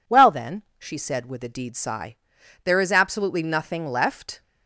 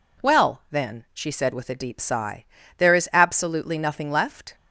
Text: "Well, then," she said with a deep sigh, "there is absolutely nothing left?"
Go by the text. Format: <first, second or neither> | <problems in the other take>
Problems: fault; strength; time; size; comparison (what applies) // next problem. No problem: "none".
second | says "deed" for "deep"; at 1.4 s